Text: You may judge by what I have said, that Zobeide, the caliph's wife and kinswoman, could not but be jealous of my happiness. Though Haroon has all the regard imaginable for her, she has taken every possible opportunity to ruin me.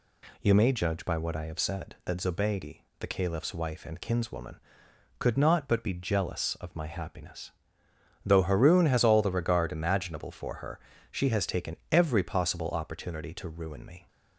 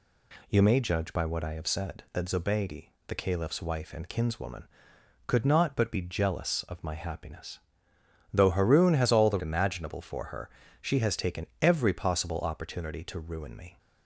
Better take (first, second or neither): first